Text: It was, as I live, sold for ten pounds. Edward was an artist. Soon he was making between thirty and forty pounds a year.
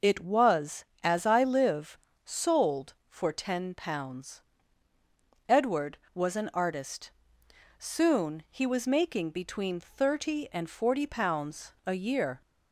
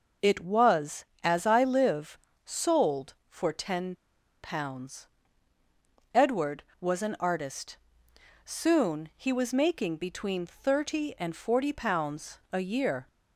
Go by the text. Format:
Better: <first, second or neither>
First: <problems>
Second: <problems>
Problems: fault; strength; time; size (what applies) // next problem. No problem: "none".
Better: first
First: none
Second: pauses between "ten" and "pounds"; noticeable; at 3.9 s; 0.47 s long